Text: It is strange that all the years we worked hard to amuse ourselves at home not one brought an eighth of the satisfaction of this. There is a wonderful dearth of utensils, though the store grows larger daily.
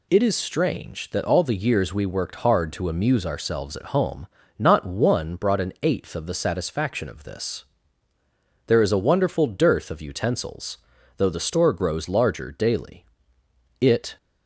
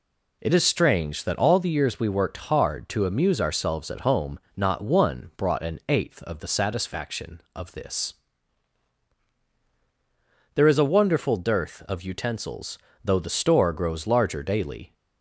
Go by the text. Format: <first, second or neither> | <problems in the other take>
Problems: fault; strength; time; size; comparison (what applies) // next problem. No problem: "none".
second | pauses between "home" and "not"; slight; at 4.2 s; 0.34 s long; slight in the second // goes on to say "It"; slight; from 13.7 s on; 0.38 s long